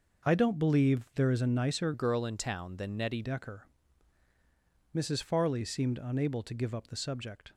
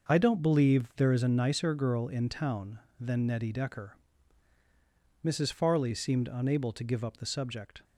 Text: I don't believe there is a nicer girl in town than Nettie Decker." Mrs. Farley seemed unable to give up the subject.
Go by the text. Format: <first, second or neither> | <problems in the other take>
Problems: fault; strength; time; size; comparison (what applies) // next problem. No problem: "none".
second | changes voice from "girl" to "Nettie"; from 1.9 to 3.2 s; 1.3 s long